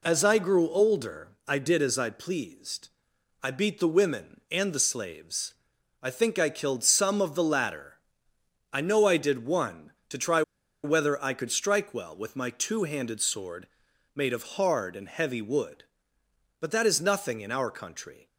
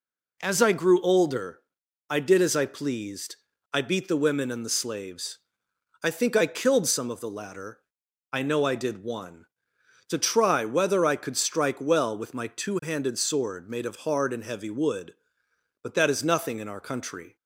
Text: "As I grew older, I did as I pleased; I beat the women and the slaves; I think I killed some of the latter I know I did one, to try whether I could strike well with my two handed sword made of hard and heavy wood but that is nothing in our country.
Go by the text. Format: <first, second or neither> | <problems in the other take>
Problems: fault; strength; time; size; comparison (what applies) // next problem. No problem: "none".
second | pauses between "latter" and "I"; noticeable; at 7.9 s; 0.70 s long; noticeable in the second // pauses between "try" and "whether"; at 10.4 s; 0.42 s long // pauses between "sword" and "made"; noticeable; at 13.6 s; 0.46 s long // pauses between "of" and "hard"; slight; at 14.4 s; 0.16 s long